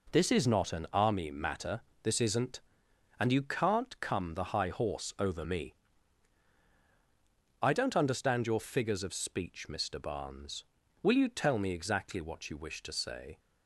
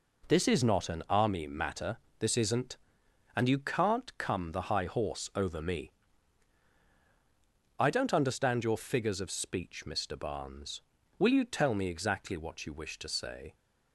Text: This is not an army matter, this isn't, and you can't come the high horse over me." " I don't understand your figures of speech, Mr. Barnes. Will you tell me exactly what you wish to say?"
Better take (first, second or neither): neither